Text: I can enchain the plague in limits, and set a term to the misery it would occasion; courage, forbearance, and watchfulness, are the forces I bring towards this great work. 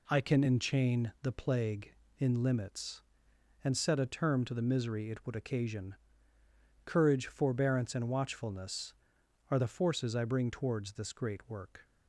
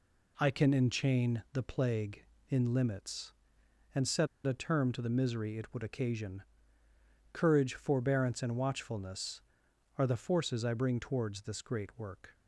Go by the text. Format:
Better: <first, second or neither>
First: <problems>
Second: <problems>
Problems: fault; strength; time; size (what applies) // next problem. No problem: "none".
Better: first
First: none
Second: pauses between "set" and "a"; slight; at 4.2 s; 0.19 s long